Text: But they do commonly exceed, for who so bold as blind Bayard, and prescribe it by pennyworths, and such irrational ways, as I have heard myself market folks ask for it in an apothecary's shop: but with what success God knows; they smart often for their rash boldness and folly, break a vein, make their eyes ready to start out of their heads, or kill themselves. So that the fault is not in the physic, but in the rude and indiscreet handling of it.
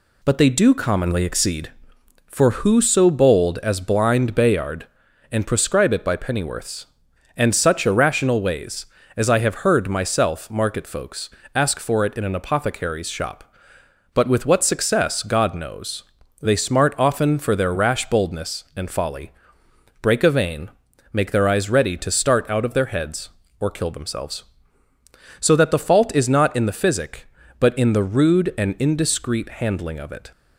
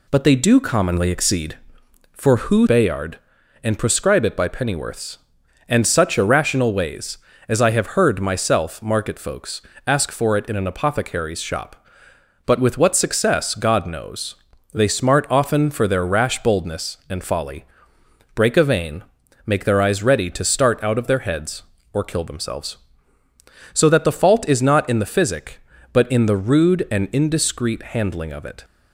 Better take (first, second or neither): first